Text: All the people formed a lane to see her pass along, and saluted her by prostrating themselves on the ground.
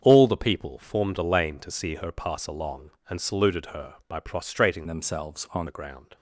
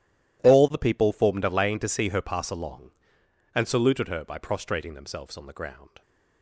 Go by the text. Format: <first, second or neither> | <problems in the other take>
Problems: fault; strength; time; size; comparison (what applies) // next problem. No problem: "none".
second | starts louder than the rest; strong; until 1.0 s; 7.5 dB // changes voice from "themselves" to "on"; from 4.8 to 5.6 s; 0.8 s long